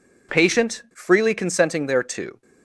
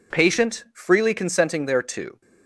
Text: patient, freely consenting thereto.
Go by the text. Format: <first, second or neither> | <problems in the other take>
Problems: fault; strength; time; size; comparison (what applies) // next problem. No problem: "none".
neither | none